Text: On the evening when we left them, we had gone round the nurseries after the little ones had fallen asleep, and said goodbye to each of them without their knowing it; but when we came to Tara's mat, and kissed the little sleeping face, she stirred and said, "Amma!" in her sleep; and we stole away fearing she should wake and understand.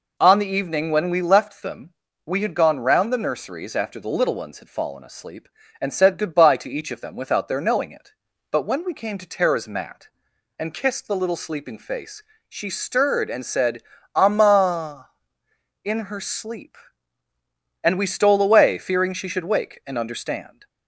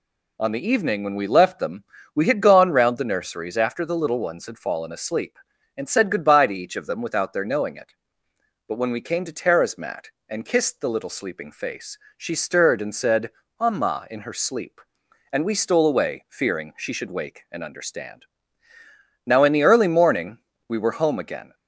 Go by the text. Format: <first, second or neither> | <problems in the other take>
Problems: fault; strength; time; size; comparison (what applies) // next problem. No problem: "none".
first | goes on to say "Now in the early morning we were home again"; strong; from 19.2 s on; 2.2 s long